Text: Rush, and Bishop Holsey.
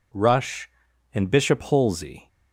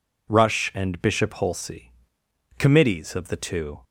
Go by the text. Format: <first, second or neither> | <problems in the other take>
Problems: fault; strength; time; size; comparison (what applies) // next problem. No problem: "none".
first | goes on to say "Committees of the Two"; noticeable; from 2.5 s on; 1.2 s long